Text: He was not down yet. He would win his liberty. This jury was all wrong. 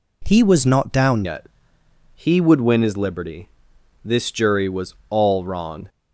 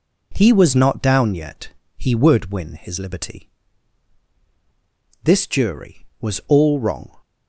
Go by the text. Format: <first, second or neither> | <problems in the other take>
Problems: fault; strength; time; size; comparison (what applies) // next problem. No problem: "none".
second | changes voice at "yet"; from 1.2 s on; 4.6 s long // pauses between "was" and "all"; slight; at 4.9 s; 0.16 s long